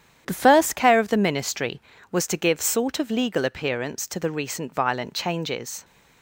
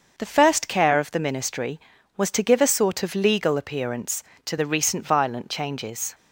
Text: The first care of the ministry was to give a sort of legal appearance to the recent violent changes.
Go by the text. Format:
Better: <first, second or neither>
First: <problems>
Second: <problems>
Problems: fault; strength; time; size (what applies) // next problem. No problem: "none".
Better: second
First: starts louder than the rest; strong; until 1.2 s; 9.5 dB // skips "a"; at 2.5 s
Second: starts louder than the rest; until 1.1 s; 6.5 dB